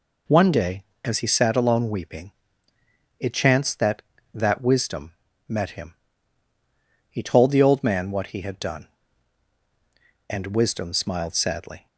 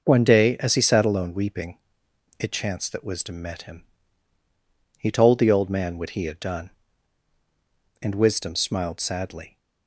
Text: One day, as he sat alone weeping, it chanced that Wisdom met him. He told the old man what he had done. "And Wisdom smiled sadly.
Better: second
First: says "that" twice; at 4.3 s // pauses between "Wisdom" and "met"; slight; at 5.1 s; 0.34 s long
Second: none

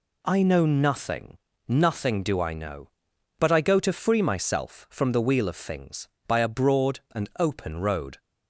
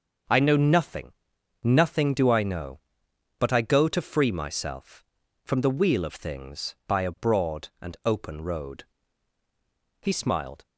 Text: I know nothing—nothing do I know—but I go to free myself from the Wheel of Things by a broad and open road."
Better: first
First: none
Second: starts louder than the rest; until 1.8 s; 6.5 dB // goes on to say "He smiled"; noticeable; from 10.0 s on; 0.64 s long

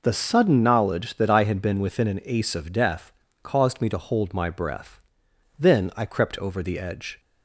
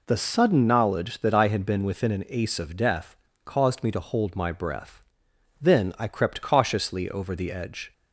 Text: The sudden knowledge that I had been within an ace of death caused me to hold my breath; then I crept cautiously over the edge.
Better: second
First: pauses between "death" and "caused"; slight; at 3.1 s; 0.32 s long // skips "cautiously"; at 6.3 s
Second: pauses between "death" and "caused"; slight; at 3.1 s; 0.30 s long

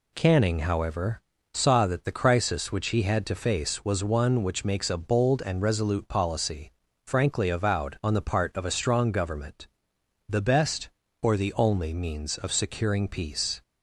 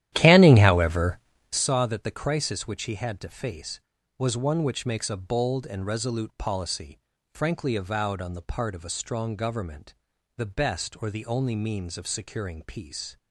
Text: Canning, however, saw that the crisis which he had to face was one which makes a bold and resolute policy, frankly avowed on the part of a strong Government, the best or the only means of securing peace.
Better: first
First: none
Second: starts louder than the rest; strong; until 1.6 s; 12.5 dB

